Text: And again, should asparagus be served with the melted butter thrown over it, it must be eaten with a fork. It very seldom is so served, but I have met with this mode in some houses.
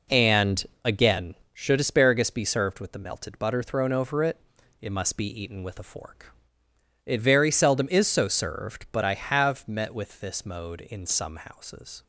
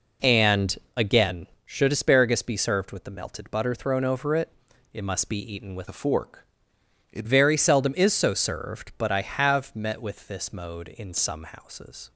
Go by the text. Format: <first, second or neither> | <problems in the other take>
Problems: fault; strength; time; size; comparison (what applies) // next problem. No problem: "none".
first | pauses between "And" and "again"; slight; at 0.7 s; 0.18 s long; slight in the first // changes voice from "a" to "It"; from 5.8 to 7.2 s; 1.4 s long